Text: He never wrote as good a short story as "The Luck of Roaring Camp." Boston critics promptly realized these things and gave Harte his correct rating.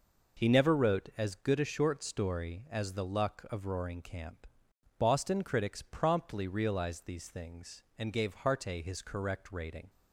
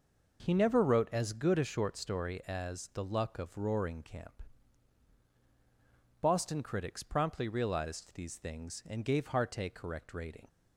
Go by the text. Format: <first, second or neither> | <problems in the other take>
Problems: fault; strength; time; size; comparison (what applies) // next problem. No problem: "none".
first | skips "his"; at 9.7 s